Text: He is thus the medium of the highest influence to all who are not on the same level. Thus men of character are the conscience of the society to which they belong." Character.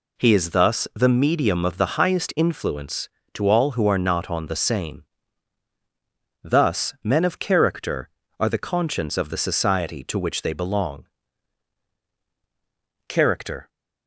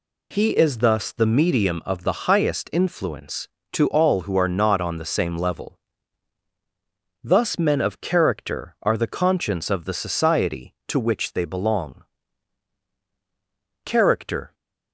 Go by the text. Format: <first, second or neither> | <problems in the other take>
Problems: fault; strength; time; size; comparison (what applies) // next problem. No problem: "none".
second | skips "level"; at 5.7 s